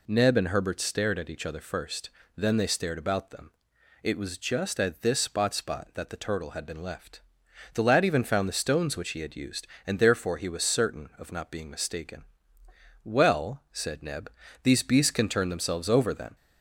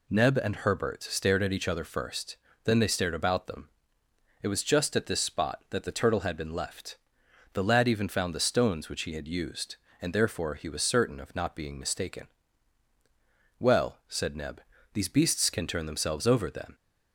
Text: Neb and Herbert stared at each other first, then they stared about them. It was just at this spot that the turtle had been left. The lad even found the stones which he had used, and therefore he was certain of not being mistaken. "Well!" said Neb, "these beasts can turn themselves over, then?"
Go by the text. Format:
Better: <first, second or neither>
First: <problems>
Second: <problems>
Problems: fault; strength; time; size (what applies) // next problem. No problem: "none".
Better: second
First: says "spot" twice; at 5.5 s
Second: none